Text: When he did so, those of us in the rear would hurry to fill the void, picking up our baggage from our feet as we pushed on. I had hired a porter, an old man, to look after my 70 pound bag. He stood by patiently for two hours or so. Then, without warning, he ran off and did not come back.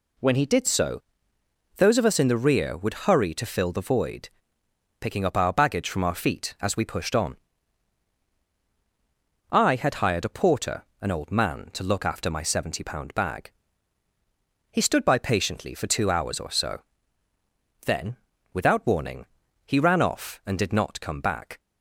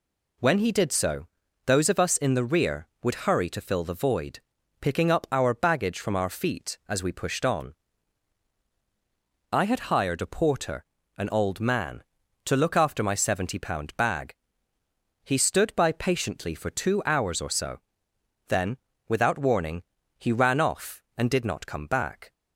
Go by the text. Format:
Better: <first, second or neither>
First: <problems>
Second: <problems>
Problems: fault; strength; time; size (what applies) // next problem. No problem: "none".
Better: neither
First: none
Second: none